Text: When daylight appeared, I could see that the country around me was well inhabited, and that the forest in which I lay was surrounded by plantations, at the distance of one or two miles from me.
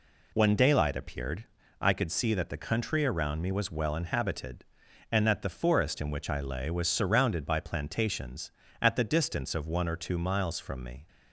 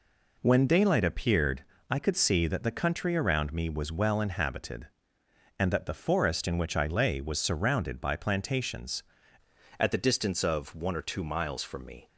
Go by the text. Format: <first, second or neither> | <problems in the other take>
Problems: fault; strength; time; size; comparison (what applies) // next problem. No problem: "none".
first | changes voice at "at"; from 9.7 s on; 2.3 s long